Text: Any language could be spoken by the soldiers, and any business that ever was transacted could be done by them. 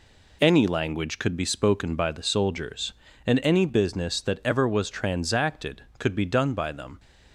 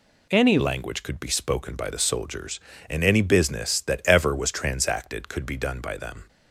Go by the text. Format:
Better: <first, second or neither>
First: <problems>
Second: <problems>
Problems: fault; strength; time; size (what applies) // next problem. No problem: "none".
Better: first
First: none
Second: changes voice at "language"; from 0.5 s on; 5.7 s long